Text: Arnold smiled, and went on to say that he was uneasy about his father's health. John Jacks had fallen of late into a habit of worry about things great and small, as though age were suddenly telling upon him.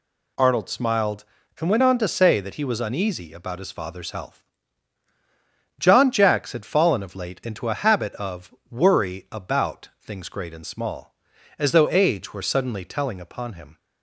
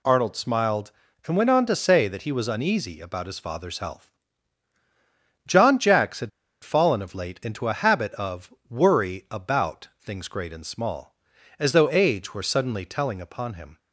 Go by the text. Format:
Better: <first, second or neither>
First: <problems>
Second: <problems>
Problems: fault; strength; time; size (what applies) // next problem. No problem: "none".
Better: first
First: pauses between "of" and "worry"; slight; at 8.5 s; 0.18 s long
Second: pauses between "had" and "fallen"; slight; at 6.2 s; 0.33 s long // pauses between "of" and "worry"; slight; at 8.5 s; 0.18 s long